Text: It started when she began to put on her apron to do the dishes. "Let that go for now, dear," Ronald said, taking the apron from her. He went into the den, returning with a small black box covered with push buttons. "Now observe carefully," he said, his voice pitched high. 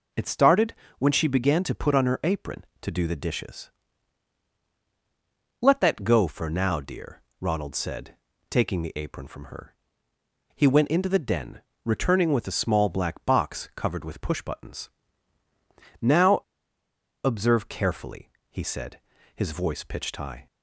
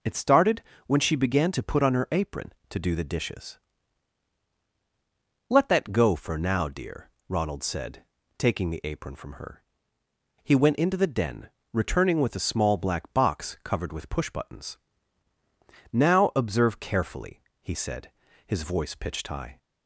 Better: second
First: pauses between "started" and "when"; slight; at 0.7 s; 0.24 s long // pauses between "Now" and "observe"; noticeable; at 16.4 s; 0.83 s long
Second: pauses between "started" and "when"; slight; at 0.6 s; 0.24 s long

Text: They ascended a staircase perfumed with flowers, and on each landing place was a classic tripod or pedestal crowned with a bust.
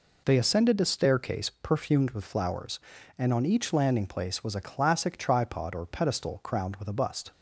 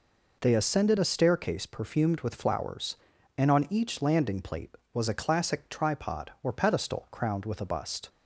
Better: first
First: none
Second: says "plate" for "place"; at 4.4 s

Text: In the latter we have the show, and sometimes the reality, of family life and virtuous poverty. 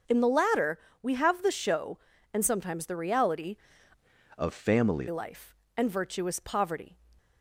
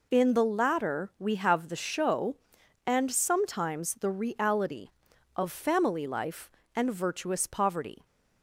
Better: second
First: starts louder than the rest; until 1.3 s; 6.5 dB // pauses between "latter" and "we"; slight; at 0.7 s; 0.24 s long // changes voice from "of" to "family"; from 4.3 to 5.0 s; 0.7 s long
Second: none

